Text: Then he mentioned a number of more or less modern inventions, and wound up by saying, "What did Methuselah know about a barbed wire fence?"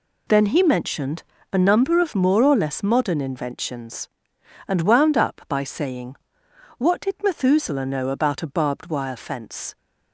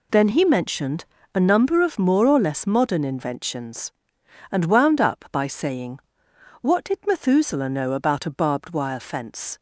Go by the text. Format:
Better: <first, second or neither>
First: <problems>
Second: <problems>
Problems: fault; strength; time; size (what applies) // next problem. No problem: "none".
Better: neither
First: pauses between "mentioned" and "a"; slight; at 1.2 s; 0.30 s long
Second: pauses between "mentioned" and "a"; slight; at 1.0 s; 0.30 s long